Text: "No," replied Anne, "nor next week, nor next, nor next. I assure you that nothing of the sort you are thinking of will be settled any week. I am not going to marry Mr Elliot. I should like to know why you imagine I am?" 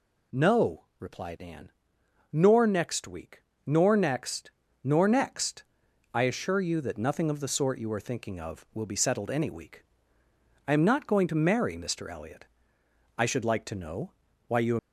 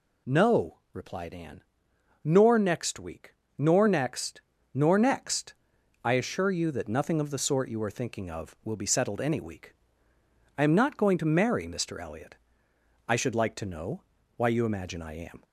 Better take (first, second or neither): second